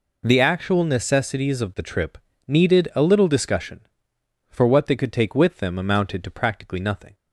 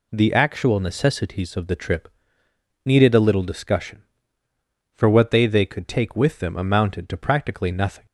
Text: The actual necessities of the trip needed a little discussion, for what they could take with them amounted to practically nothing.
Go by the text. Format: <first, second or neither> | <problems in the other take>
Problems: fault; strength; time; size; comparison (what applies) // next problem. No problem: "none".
first | pauses between "trip" and "needed"; noticeable; at 2.0 s; 0.74 s long; slight in the first // says "they" twice; at 5.4 s